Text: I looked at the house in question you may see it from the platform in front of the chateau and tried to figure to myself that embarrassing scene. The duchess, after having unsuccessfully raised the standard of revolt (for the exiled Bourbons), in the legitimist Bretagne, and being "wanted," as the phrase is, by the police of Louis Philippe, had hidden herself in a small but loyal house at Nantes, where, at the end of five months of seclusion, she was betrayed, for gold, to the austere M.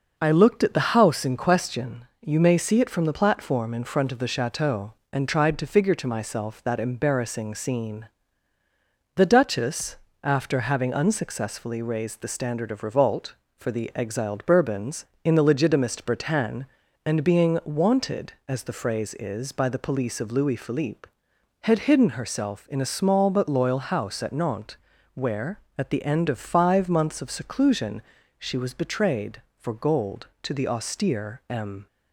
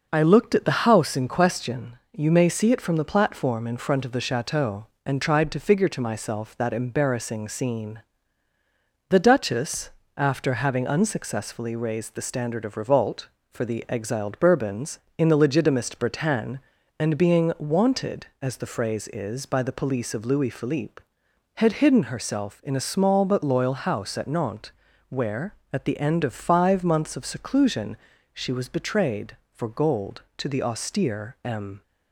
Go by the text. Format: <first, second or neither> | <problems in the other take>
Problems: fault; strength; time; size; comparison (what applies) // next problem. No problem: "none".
neither | pauses between "question" and "you"; slight; the same in both